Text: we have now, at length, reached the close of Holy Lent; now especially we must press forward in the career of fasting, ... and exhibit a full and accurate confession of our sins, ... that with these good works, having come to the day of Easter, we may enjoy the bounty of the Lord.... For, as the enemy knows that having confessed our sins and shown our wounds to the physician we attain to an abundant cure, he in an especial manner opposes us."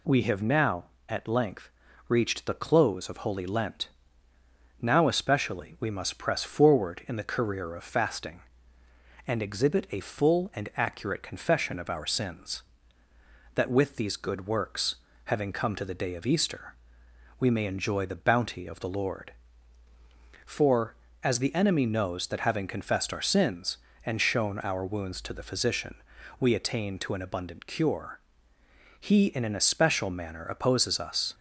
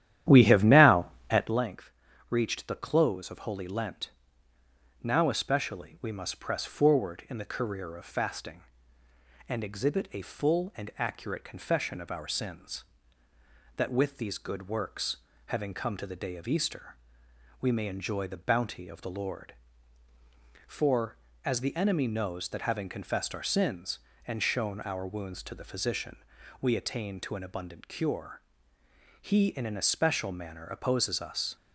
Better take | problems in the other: first | starts louder than the rest; strong; until 1.6 s; 11.5 dB // pauses between "physician" and "we"; at 26.1 s; 0.42 s long; also in the first

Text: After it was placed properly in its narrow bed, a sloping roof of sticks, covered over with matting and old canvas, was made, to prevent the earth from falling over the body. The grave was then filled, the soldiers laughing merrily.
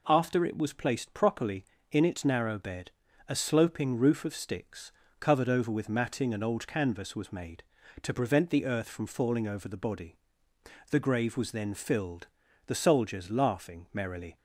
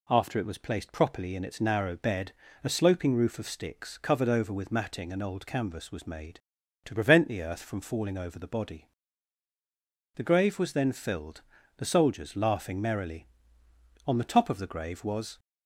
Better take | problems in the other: first | goes on to say "On the top of the grave was"; from 14.0 s on; 1.3 s long

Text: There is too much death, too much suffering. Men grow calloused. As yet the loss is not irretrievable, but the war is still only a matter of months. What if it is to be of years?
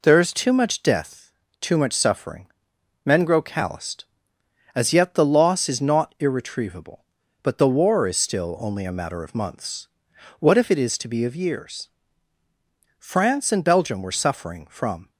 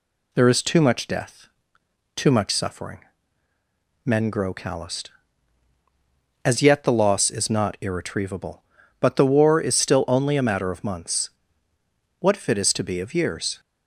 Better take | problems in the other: second | goes on to say "France and Belgium were suffering from"; strong; from 12.9 s on; 2.1 s long

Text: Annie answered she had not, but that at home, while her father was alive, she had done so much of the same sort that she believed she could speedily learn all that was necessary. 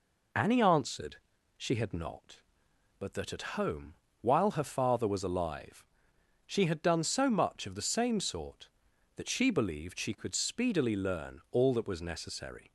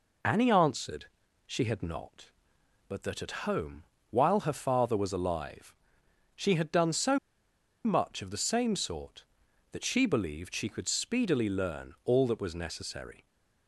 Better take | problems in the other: first | pauses between "answered" and "she"; at 1.0 s; 0.42 s long; also in the first // pauses between "so" and "much"; noticeable; at 7.1 s; 0.67 s long

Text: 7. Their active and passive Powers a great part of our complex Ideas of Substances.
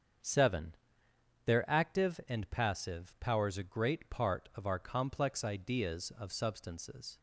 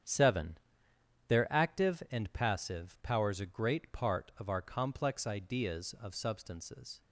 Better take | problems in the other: first | gets quieter; strong; throughout; 9.5 dB // starts louder than the rest; strong; until 1.7 s; 8.5 dB; also in the first

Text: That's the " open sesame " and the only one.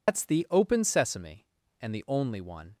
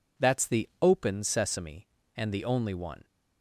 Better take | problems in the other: second | loses the start of "That's"; at 0.0 s; 120 ms

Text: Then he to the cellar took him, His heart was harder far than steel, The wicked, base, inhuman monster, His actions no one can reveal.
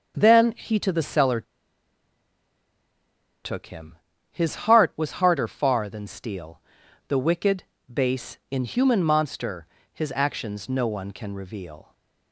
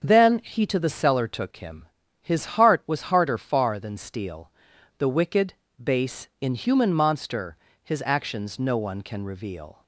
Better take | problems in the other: second | starts louder than the rest; until 1.1 s; 7 dB; also in the second // pauses between "cellar" and "took"; strong; at 1.4 s; 2.0 s long // pauses between "His" and "heart"; slight; at 4.5 s; 0.16 s long; slight in the second

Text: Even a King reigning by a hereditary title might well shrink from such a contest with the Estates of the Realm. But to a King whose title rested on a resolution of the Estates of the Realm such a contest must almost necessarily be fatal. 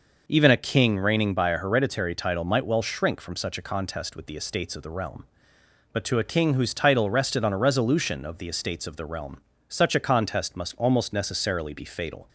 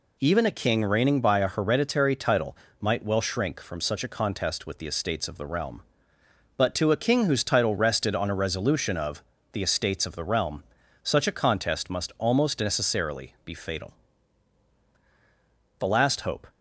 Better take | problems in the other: first | pauses between "title" and "might"; slight; at 2.5 s; 0.24 s long // pauses between "of" and "the"; slight; at 9.2 s; 0.30 s long // pauses between "Realm" and "such"; at 10.6 s; 0.40 s long; slight in the first // goes on to say "The last hope"; noticeable; from 15.7 s on; 0.68 s long

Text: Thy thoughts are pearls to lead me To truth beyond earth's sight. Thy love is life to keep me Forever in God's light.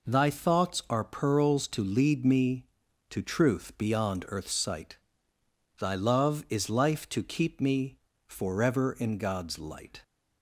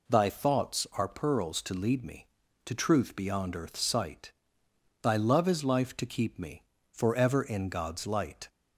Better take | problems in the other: neither | pauses between "me" and "Forever"; slight; the same in both

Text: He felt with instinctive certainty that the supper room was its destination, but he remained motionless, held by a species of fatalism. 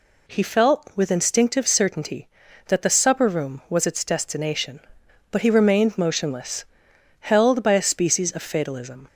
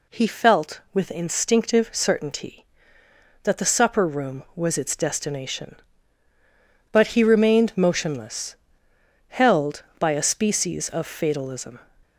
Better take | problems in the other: neither | none

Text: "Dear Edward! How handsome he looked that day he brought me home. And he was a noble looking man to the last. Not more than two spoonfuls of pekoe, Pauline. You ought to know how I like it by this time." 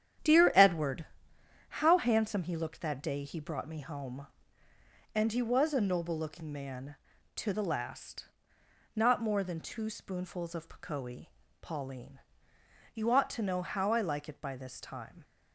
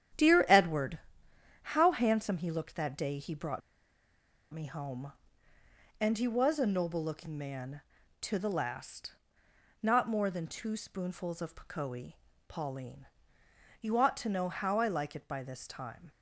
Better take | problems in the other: first | starts louder than the rest; strong; until 1.9 s; 10.5 dB; strong in the first // pauses between "brought" and "me"; noticeable; at 3.6 s; 0.93 s long

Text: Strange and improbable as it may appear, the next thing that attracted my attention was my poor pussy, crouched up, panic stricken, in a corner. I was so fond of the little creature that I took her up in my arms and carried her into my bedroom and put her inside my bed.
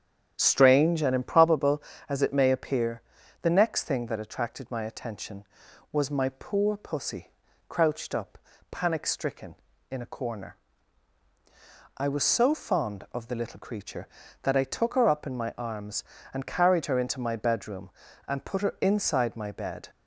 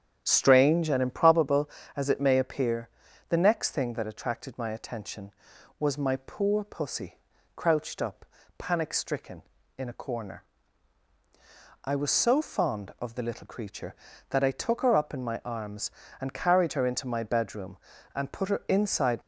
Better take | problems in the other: first | starts louder than the rest; strong; until 1.2 s; 8.5 dB; strong in the first // stops before "my bed"; at 19.2 s

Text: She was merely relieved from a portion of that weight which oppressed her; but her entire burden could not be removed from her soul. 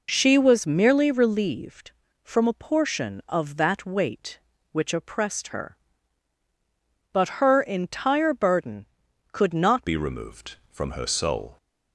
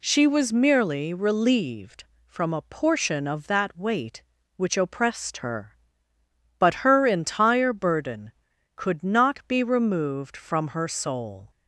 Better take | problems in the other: second | changes voice at "be"; from 9.8 s on; 1.7 s long

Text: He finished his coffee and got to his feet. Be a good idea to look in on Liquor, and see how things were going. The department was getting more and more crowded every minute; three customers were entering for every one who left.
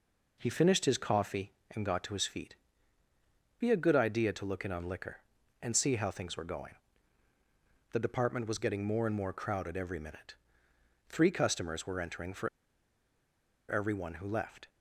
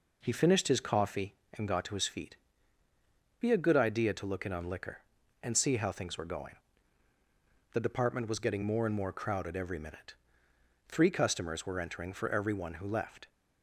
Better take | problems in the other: second | pauses between "for" and "every"; at 12.4 s; 1.1 s long

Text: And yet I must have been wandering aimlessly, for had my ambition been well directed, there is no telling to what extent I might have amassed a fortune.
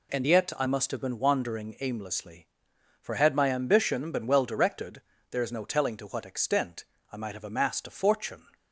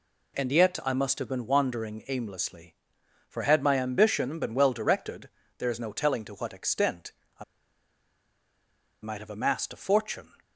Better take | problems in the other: first | pauses between "extent" and "I"; slight; at 7.1 s; 0.26 s long; slight in the first // pauses between "I" and "might"; strong; at 7.4 s; 1.5 s long

